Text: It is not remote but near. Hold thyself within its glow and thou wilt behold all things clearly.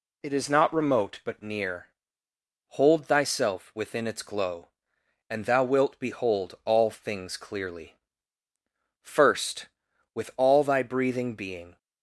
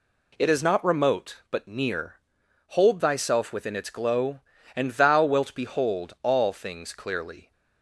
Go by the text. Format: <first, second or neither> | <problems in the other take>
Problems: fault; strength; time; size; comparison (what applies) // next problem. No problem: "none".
second | goes on to say "First with all thy breathing being"; strong; from 9.0 s on; 2.7 s long